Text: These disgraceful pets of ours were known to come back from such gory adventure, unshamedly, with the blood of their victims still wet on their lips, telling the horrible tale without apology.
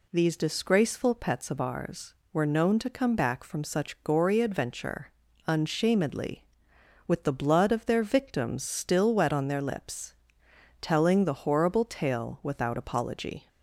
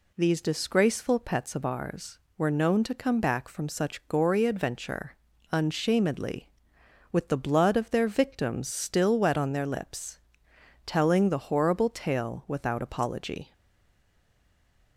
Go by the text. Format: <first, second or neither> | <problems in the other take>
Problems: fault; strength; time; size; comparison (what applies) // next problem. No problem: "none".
first | stays silent after the last word; noticeable; from 13.5 s on; 1.4 s long